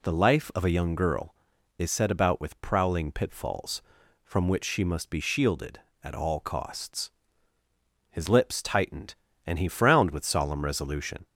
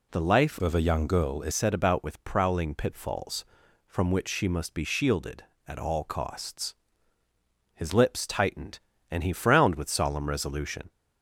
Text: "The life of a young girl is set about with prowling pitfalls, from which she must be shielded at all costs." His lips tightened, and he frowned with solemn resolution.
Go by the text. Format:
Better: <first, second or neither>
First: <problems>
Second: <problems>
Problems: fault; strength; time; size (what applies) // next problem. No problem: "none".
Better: first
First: none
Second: changes voice from "of" to "is"; from 0.6 to 1.5 s; 0.9 s long